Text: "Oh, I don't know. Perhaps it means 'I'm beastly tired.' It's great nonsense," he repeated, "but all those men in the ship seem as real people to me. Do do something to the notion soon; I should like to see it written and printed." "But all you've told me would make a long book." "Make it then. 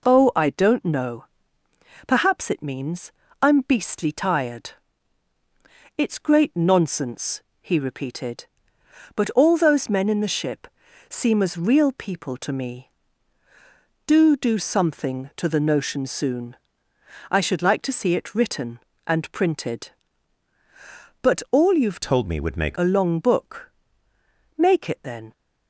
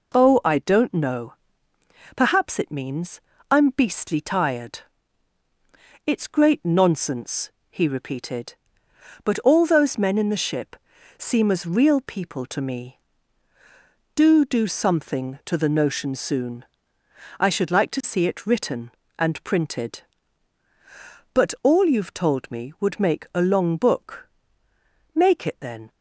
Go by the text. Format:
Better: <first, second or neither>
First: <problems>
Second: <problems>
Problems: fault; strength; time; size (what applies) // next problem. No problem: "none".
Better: second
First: pauses between "means" and "I'm"; slight; at 3.1 s; 0.28 s long // pauses between "ship" and "seem"; at 10.6 s; 0.40 s long // changes voice from "told" to "make"; from 22.0 to 22.7 s; 0.7 s long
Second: pauses between "means" and "I'm"; slight; at 3.2 s; 0.28 s long // pauses between "ship" and "seem"; at 10.7 s; 0.40 s long